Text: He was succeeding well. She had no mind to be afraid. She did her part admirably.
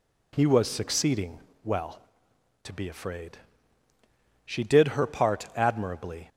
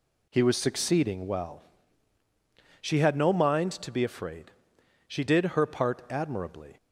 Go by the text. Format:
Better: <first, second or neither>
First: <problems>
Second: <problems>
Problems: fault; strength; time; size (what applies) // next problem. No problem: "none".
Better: second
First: pauses between "succeeding" and "well"; slight; at 1.3 s; 0.24 s long // skips "She had no mind"; at 2.3 s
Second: none